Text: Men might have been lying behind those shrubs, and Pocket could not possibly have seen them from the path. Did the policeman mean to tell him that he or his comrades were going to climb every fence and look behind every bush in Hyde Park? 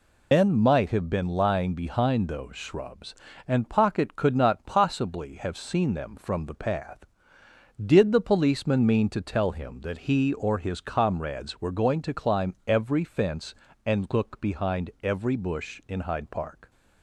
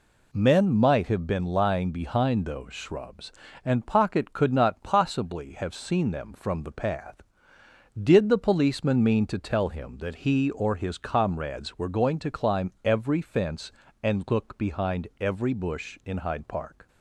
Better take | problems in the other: second | loses the start of "Men"; at 0.3 s; 150 ms

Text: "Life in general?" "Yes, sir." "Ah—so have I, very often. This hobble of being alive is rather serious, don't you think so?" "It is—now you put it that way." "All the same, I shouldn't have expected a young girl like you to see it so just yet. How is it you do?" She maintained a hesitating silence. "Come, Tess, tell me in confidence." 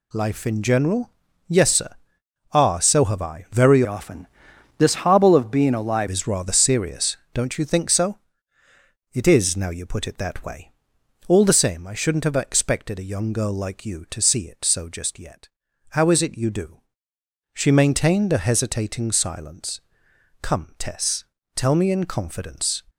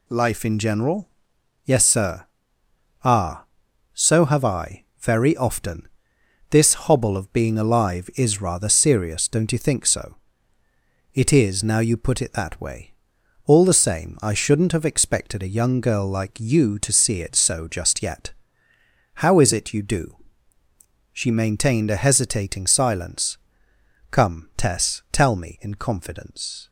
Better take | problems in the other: second | changes voice from "often" to "alive"; from 3.8 to 6.0 s; 2.2 s long

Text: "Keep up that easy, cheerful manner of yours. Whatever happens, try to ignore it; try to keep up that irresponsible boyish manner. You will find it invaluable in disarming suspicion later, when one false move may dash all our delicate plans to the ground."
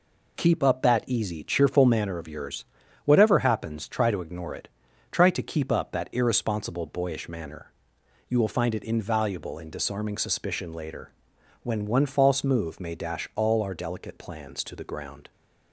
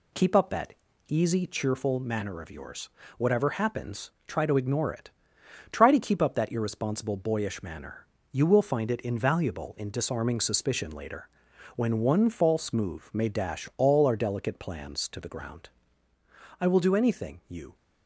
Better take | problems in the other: first | pauses between "that" and "easy"; slight; at 0.7 s; 0.34 s long // goes on to say "I will do anything you"; noticeable; from 16.5 s on; 1.1 s long

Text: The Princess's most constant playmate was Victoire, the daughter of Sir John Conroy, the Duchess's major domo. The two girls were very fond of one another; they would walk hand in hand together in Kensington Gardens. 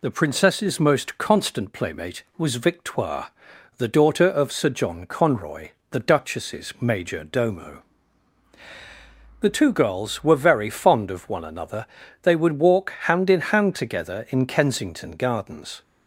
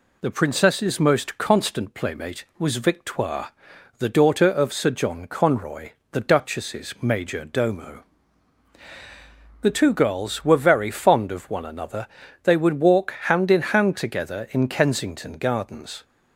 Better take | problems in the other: neither | none

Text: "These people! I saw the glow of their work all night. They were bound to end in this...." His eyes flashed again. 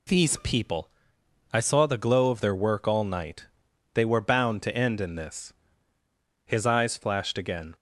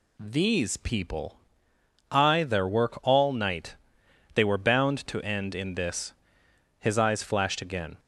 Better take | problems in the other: first | skips "saw the glow of"; at 2.4 s

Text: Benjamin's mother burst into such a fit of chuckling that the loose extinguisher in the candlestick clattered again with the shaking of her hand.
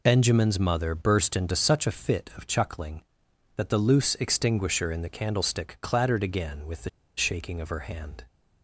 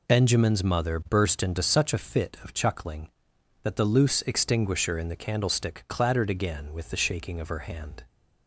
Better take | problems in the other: second | pauses between "the" and "shaking"; slight; at 6.8 s; 0.27 s long

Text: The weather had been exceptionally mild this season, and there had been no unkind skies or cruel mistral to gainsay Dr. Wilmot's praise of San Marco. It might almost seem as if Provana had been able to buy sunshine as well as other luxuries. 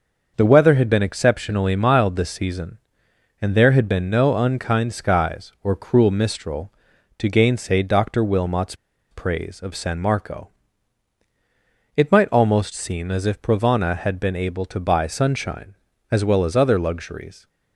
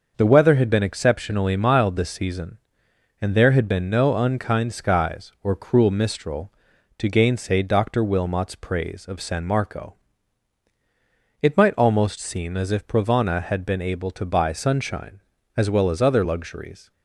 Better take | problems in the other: second | starts louder than the rest; noticeable; until 1.3 s; 6 dB; noticeable in the second // pauses between "Wilmot's" and "praise"; at 8.7 s; 0.37 s long

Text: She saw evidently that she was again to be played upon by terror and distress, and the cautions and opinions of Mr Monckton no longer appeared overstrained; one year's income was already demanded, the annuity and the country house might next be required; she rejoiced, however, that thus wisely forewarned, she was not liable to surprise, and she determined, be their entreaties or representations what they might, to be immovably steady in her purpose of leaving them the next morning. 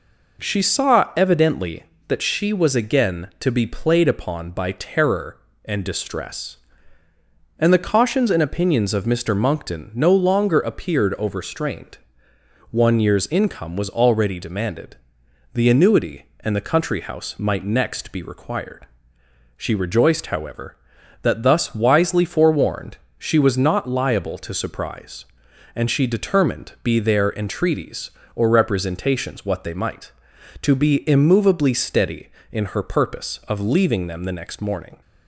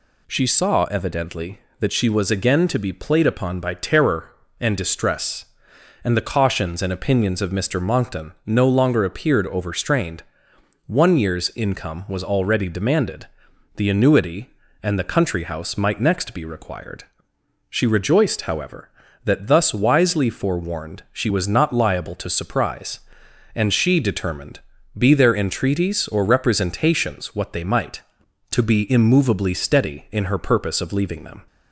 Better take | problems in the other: first | stops before "the next morning"; at 31.4 s

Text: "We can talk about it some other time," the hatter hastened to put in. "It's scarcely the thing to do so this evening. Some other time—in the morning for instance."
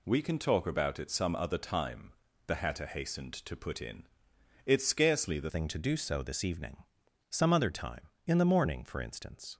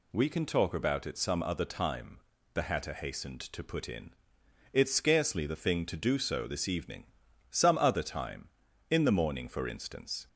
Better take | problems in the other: second | changes voice at "thing"; from 5.4 s on; 4.1 s long

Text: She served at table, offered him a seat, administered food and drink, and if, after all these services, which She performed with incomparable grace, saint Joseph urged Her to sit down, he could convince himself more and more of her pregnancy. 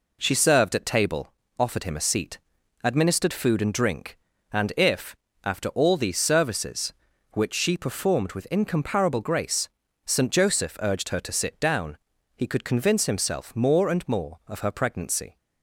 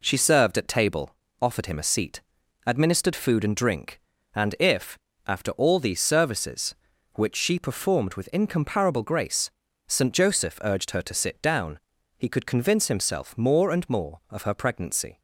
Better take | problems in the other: neither | none

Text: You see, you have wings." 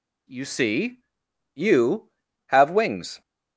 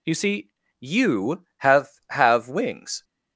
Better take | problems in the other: first | says "have" twice; at 2.0 s

